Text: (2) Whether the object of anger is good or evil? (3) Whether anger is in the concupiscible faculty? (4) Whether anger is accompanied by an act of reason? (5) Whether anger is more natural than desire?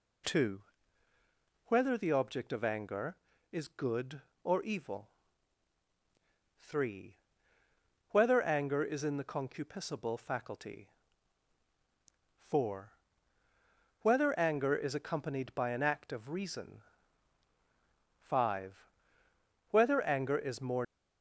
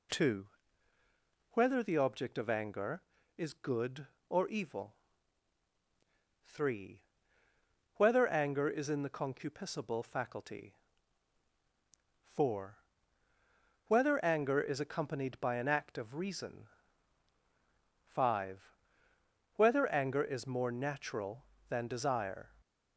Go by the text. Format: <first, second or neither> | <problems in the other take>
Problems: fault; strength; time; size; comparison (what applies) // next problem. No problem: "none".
second | stops before "natural than desire"; at 20.8 s